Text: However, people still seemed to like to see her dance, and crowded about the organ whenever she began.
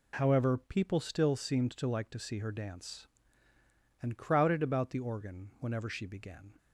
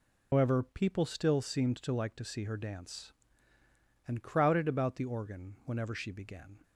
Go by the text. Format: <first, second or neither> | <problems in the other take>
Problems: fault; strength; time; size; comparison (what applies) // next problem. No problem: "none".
first | loses the start of "However"; at 0.3 s; 135 ms